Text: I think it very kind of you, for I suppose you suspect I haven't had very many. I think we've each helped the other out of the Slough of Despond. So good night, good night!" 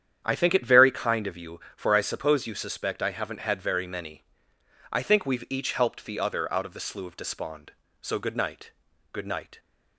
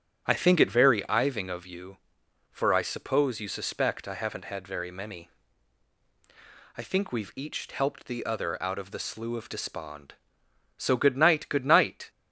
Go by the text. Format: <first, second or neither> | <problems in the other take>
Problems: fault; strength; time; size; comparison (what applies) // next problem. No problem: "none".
first | starts louder than the rest; strong; until 1.2 s; 9 dB; strong in the first // says "iving" for "kind"; at 1.0 s